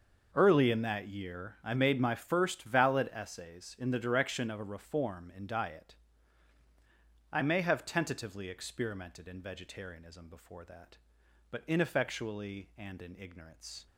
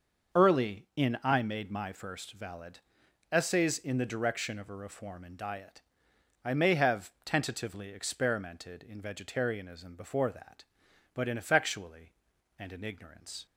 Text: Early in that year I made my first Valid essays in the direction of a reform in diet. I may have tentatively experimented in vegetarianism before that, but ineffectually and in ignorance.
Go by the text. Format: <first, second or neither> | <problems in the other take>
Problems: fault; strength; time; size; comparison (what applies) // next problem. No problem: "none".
first | starts louder than the rest; until 1.5 s; 6.5 dB; noticeable in the first // skips "that year"; at 1.2 s // pauses between "Valid" and "essays"; noticeable; at 2.7 s; 0.52 s long